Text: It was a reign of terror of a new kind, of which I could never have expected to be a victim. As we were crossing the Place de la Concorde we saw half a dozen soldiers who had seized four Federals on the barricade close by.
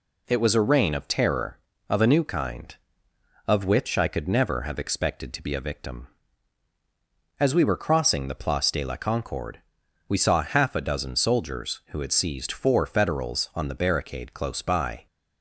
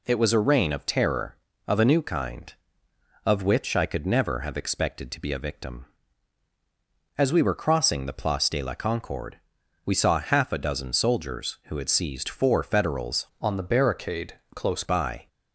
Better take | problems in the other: first | pauses between "Concorde" and "we"; noticeable; at 9.3 s; 0.46 s long; noticeable in the first // changes voice from "on" to "close"; from 13.4 to 14.8 s; 1.4 s long // pauses between "barricade" and "close"; slight; at 14.3 s; 0.18 s long

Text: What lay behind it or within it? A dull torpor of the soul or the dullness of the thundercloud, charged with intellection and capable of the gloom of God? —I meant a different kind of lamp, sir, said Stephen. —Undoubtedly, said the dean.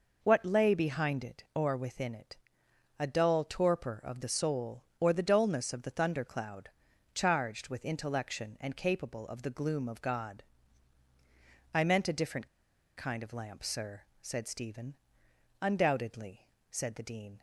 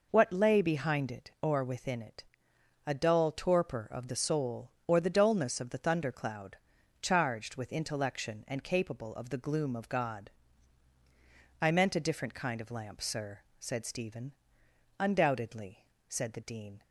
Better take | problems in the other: second | pauses between "different" and "kind"; noticeable; at 12.4 s; 0.49 s long

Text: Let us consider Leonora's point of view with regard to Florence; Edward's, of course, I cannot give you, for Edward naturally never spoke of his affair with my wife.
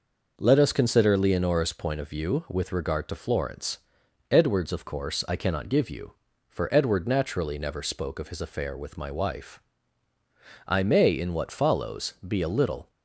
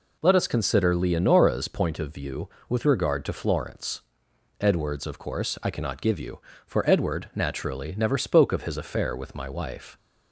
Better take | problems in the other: second | goes on to say "I may in what follows be a little"; strong; from 10.6 s on; 2.2 s long

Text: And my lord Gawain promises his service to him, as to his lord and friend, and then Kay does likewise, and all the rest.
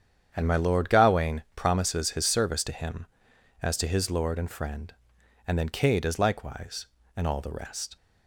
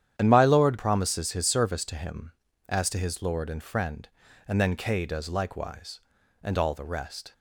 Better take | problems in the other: first | starts louder than the rest; strong; until 1.2 s; 10 dB; strong in the first // skips "Gawain"; at 0.7 s

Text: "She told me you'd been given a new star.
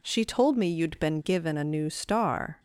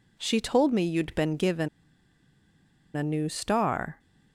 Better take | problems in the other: first | pauses between "given" and "a"; strong; at 1.6 s; 1.2 s long

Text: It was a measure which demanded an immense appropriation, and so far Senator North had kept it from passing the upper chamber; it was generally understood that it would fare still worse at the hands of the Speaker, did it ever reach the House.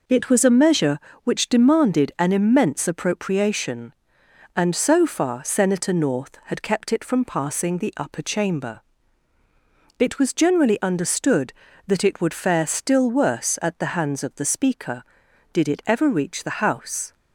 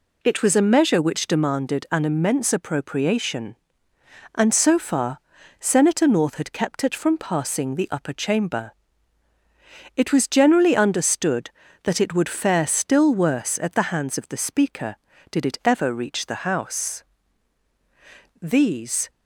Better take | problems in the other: first | pauses between "far" and "Senator"; at 5.1 s; 0.42 s long // goes on to say "These"; noticeable; from 18.4 s on; 0.68 s long

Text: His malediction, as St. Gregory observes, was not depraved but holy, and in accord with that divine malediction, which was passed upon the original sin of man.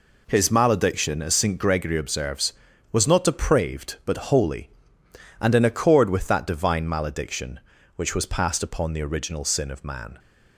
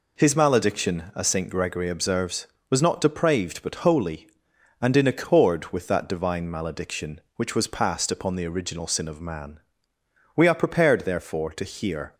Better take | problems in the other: first | goes on to say "We are prepared therefore to hear"; strong; from 10.3 s on; 1.8 s long

